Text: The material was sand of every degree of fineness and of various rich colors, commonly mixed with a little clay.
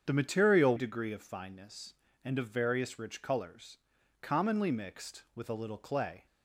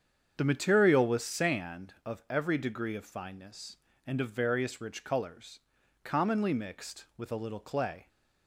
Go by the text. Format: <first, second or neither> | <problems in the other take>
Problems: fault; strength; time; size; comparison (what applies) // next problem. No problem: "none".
second | starts louder than the rest; strong; until 1.0 s; 8 dB; strong in the second // skips "was sand of every"; at 0.7 s